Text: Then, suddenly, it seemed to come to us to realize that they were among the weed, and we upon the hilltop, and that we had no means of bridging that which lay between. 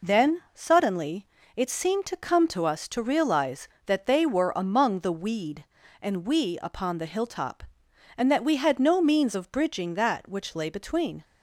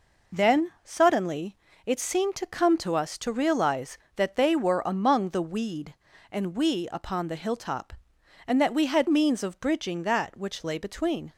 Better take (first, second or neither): first